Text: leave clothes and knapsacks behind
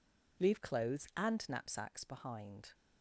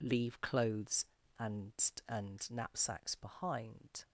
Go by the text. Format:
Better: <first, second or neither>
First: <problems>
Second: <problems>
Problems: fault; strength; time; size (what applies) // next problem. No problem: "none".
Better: first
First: none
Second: says "and" twice; at 2.0 s